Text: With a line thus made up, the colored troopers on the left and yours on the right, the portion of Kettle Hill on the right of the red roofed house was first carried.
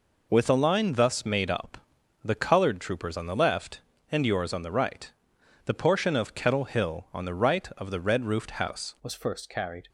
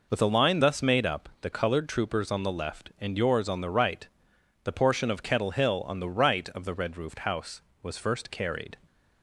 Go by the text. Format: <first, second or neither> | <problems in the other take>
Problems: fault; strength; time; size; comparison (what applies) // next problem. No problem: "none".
second | changes voice at "was"; from 9.0 s on; 0.8 s long